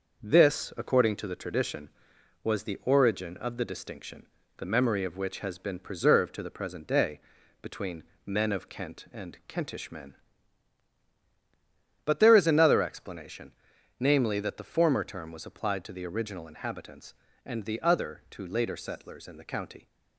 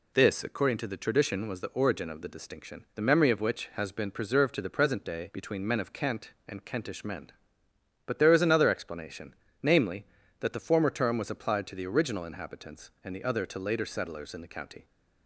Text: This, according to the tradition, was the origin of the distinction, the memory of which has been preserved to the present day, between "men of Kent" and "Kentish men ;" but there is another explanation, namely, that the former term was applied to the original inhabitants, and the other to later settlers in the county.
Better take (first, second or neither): second